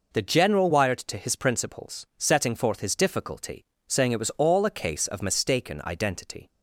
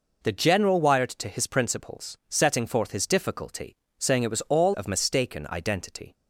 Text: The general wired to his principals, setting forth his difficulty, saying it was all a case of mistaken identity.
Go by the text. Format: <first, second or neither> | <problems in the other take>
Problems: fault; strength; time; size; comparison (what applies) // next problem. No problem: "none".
first | skips "a case"; at 4.7 s